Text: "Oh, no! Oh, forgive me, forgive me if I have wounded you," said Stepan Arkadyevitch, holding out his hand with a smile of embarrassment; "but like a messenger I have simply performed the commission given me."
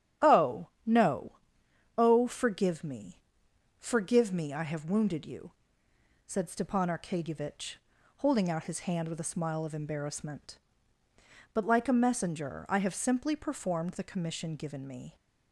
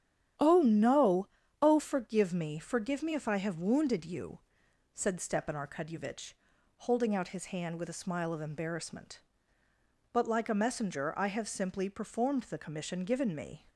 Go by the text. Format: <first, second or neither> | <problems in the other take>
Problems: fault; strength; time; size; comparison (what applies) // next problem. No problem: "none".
second | starts louder than the rest; strong; until 2.0 s; 10 dB; strong in the second // skips "if"; at 4.5 s